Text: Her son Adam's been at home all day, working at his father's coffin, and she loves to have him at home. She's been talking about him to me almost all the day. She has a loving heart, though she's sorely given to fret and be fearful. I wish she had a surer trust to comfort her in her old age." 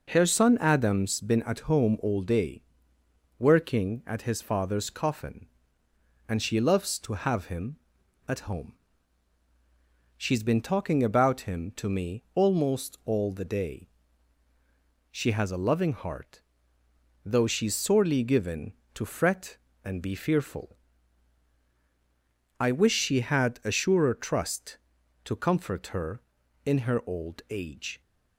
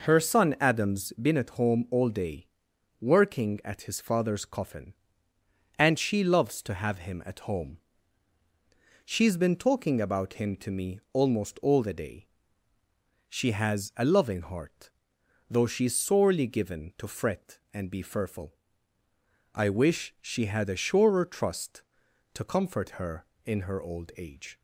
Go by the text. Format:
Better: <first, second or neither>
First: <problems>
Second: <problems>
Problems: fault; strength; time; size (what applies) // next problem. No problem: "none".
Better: neither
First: none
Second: none